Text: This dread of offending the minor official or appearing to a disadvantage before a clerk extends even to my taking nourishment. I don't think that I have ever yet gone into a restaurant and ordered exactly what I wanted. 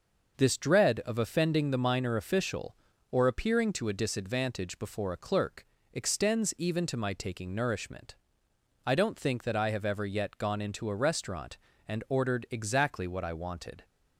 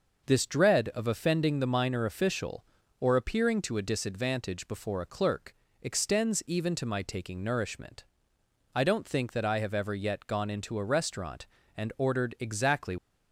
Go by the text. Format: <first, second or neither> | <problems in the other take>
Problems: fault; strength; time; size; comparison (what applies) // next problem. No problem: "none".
first | pauses between "clerk" and "extends"; slight; at 5.5 s; 0.28 s long; slight in the first // stops before "what I wanted"; at 12.9 s